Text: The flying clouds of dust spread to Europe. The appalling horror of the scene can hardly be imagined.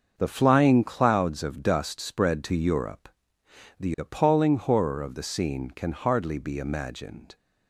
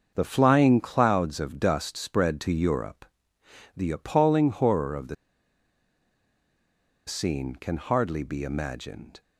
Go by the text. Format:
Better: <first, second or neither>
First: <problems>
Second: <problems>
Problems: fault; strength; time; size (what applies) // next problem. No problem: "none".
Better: first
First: starts louder than the rest; until 1.1 s; 6.5 dB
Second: starts louder than the rest; until 1.1 s; 6.5 dB // pauses between "the" and "scene"; strong; at 5.1 s; 1.9 s long